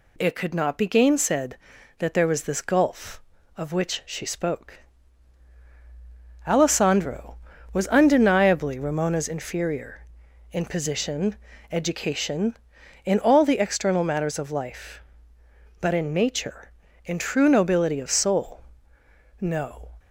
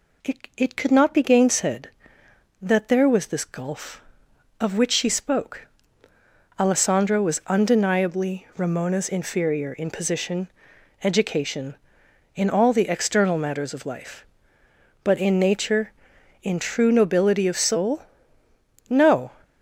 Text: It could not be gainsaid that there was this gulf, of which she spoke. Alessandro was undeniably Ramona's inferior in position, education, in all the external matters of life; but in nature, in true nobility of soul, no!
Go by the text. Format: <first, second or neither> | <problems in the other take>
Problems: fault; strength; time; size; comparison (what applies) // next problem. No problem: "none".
first | says "It" twice; at 0.5 s